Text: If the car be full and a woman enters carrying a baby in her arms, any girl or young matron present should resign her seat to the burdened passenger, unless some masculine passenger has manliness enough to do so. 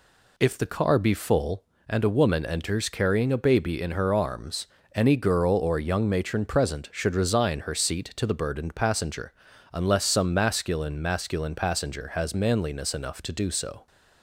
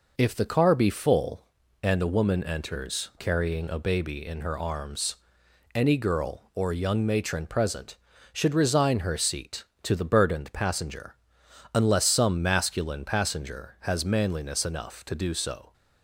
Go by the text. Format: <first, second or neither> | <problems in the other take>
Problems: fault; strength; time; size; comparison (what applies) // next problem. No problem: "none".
second | says "masculine" twice; at 11.0 s